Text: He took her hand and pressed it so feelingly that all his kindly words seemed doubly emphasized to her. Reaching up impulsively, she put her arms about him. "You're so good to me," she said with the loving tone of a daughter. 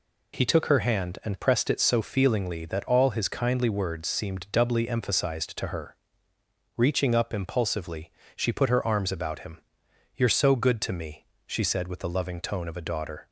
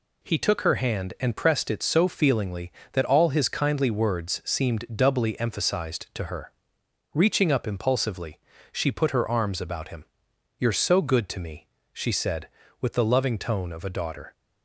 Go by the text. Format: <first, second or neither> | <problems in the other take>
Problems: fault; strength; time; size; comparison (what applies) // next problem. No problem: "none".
neither | none